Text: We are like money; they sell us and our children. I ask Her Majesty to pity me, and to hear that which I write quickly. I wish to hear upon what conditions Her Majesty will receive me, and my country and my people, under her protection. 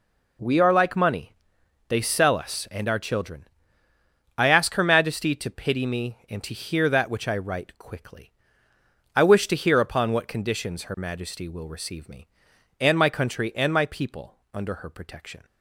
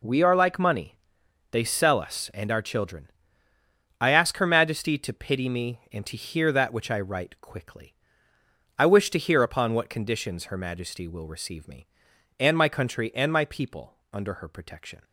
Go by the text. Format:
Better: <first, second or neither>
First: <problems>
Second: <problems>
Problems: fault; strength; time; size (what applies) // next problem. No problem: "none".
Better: neither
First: none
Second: none